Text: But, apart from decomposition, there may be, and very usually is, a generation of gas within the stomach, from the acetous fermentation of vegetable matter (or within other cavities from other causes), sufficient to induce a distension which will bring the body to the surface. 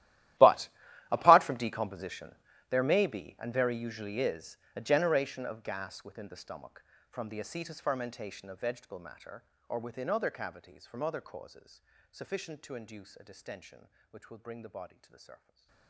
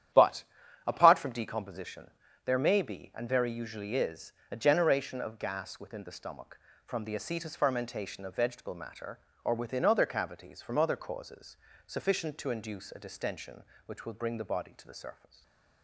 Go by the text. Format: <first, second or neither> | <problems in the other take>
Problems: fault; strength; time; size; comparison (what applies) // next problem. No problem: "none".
second | gets quieter; strong; throughout; 21 dB // starts louder than the rest; strong; until 1.8 s; 14.5 dB; strong in the second // stays silent after the last word; slight; from 15.3 s on; 0.5 s long; slight in the second